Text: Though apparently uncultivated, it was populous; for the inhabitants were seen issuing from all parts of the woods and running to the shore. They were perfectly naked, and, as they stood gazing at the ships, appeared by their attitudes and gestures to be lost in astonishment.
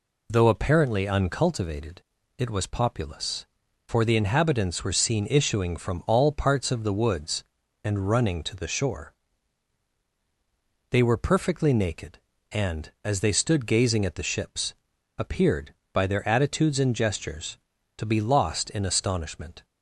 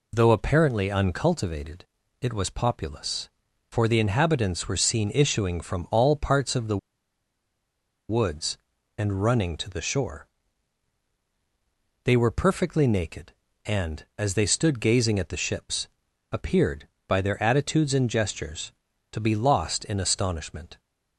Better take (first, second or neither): first